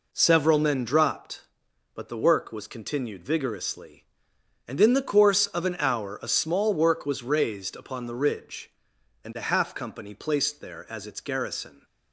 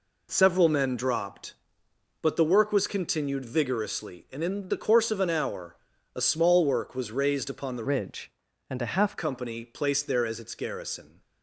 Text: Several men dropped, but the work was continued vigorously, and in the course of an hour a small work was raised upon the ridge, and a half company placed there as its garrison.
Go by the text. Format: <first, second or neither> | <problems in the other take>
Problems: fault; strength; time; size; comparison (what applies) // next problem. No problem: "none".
first | pauses between "hour" and "a"; at 5.7 s; 0.40 s long // changes voice from "ridge" to "half"; from 7.8 to 9.1 s; 1.3 s long